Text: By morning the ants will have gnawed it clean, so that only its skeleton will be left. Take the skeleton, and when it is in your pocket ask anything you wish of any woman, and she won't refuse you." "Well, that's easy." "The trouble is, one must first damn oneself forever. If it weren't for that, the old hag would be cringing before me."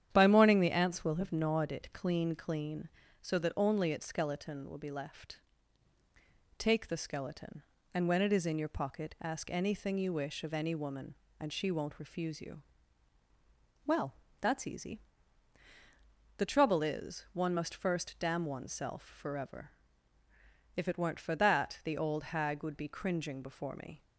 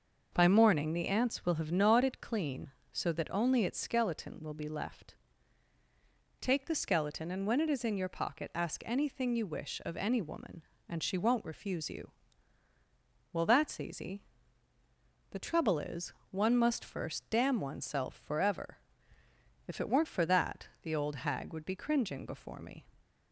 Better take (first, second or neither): second